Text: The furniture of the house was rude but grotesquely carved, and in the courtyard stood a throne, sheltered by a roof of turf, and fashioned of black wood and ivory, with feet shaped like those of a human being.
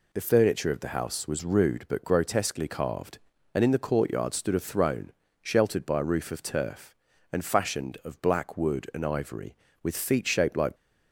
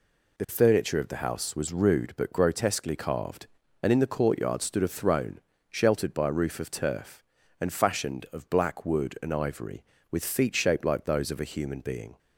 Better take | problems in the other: second | stops before "those of a human being"; at 10.7 s

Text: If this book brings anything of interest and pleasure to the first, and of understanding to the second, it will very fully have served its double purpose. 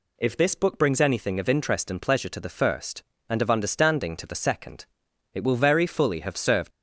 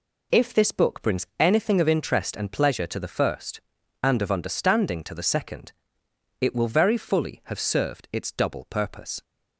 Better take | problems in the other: second | stops before "its double purpose"; at 6.7 s

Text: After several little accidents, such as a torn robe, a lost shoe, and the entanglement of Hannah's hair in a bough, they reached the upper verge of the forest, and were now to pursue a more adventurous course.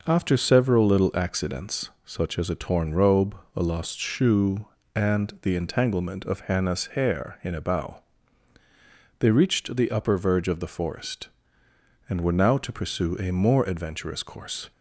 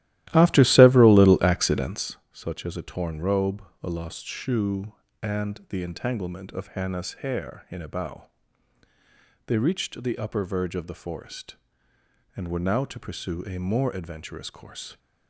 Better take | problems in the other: first | starts louder than the rest; strong; until 2.2 s; 15 dB

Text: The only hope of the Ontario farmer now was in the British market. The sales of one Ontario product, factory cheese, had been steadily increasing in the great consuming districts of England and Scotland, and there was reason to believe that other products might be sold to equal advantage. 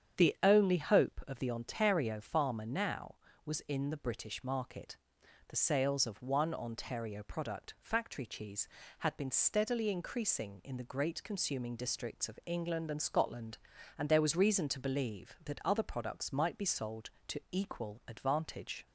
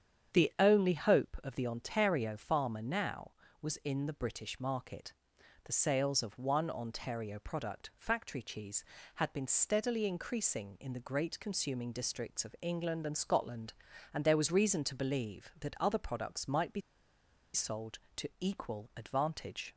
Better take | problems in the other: first | starts louder than the rest; strong; until 1.4 s; 8 dB; strong in the first // pauses between "be" and "sold"; noticeable; at 16.8 s; 0.73 s long

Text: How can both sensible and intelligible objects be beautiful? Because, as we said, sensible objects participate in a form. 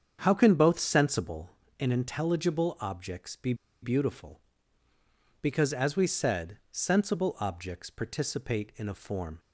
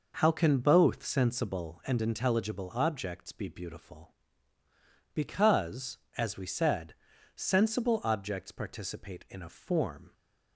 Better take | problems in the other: second | starts louder than the rest; strong; until 1.2 s; 7.5 dB // pauses between "be" and "beautiful"; slight; at 3.5 s; 0.28 s long

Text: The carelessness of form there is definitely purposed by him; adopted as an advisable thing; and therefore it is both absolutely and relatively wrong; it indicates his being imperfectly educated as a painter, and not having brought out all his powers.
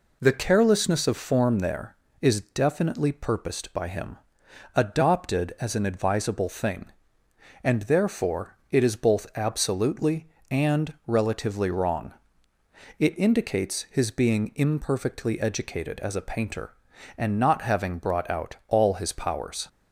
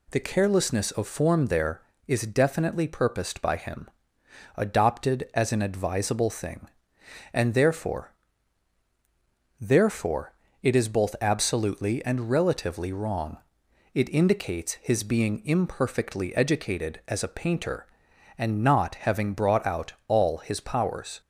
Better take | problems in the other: first | says "therefore" twice; at 9.6 s

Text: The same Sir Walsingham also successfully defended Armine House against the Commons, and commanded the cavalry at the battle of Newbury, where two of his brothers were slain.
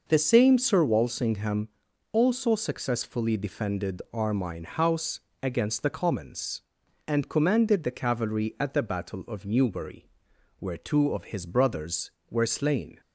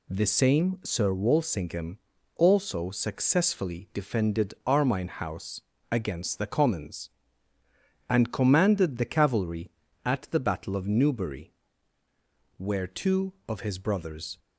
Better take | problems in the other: first | pauses between "Walsingham" and "also"; at 1.9 s; 0.38 s long; also in the first // pauses between "House" and "against"; slight; at 5.6 s; 0.30 s long; slight in the first // stops before "were slain"; at 14.3 s

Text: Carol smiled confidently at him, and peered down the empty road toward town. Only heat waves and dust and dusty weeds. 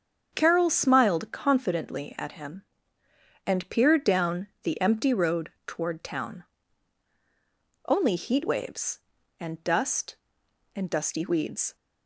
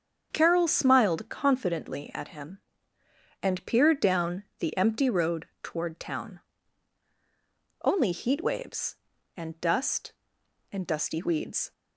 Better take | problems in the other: neither | starts louder than the rest; strong; the same in both // pauses between "down" and "the"; slight; the same in both

